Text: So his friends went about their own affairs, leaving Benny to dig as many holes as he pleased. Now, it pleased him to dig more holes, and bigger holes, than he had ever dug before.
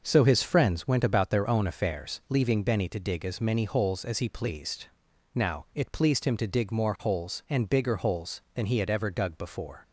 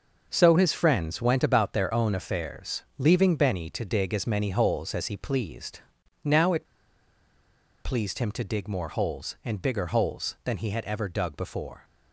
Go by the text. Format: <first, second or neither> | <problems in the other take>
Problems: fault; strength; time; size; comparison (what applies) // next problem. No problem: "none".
first | pauses between "it" and "pleased"; at 6.6 s; 1.1 s long